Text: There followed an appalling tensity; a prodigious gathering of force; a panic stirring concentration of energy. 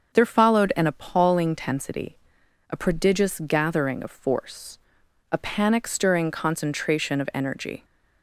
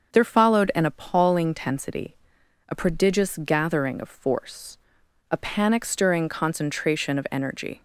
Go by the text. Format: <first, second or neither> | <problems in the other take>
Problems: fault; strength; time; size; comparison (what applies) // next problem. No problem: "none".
neither | starts louder than the rest; the same in both